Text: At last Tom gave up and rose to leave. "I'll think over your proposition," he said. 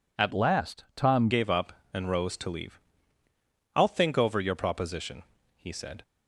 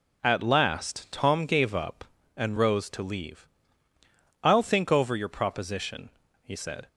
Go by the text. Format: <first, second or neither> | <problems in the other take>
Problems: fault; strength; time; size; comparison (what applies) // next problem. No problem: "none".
second | changes voice from "last" to "Tom"; from 0.3 to 1.2 s; 0.9 s long